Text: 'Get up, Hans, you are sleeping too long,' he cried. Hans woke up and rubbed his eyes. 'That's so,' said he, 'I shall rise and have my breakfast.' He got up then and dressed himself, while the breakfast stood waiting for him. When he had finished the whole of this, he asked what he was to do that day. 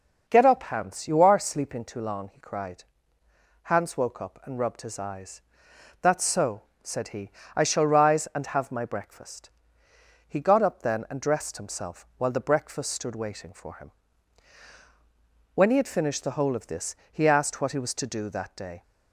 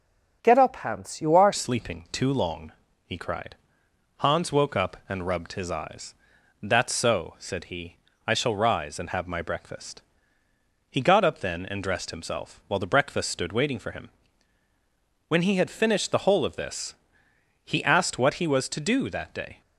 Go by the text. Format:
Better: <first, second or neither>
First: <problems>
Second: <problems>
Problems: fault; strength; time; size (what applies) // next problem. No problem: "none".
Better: first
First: none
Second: changes voice at "sleeping"; from 1.5 s on; 18.1 s long